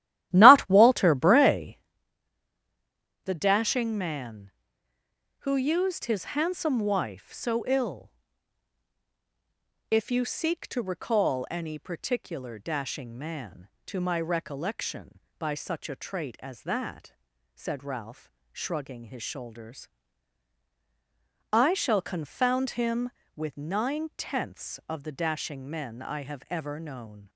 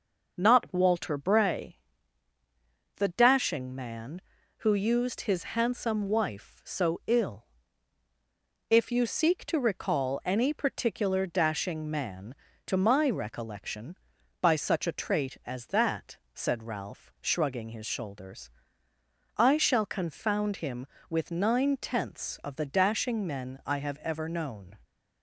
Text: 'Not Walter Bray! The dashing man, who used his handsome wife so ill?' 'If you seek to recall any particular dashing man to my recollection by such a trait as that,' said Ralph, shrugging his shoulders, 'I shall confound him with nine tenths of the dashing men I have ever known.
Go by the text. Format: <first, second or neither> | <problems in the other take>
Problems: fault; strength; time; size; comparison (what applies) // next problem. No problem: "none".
second | starts louder than the rest; strong; until 1.9 s; 14 dB